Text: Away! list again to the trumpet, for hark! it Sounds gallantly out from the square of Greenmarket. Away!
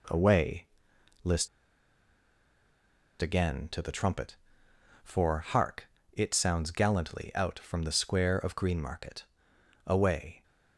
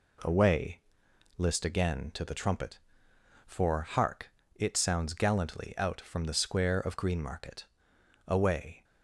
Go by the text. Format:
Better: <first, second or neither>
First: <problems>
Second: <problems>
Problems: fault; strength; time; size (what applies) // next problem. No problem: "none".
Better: second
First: pauses between "list" and "again"; strong; at 1.4 s; 1.7 s long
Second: none